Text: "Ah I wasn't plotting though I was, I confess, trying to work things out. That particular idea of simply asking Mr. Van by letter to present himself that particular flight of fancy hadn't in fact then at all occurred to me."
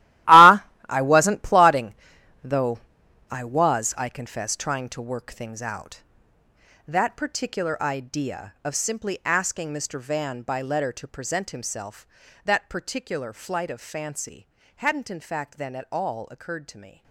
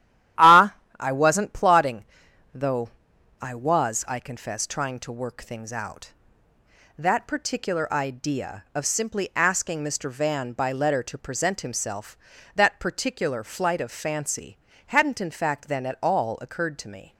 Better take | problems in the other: second | gets quieter; strong; throughout; 14 dB // starts louder than the rest; strong; until 1.5 s; 16 dB; strong in the second // pauses between "Ah" and "I"; slight; at 0.6 s; 0.24 s long; slight in the second // pauses between "plotting" and "though"; noticeable; at 1.9 s; 0.50 s long; noticeable in the second // pauses between "though" and "I"; noticeable; at 2.7 s; 0.50 s long; noticeable in the second // pauses between "fancy" and "hadn't"; slight; at 14.4 s; 0.30 s long; slight in the second

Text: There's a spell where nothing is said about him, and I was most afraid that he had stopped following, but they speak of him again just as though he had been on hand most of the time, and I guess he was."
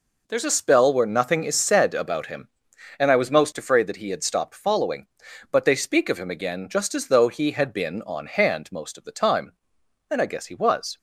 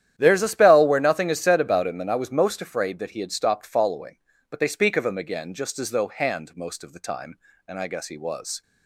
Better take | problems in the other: first | starts louder than the rest; strong; until 1.1 s; 10.5 dB // skips "he had been on"; at 6.0 s

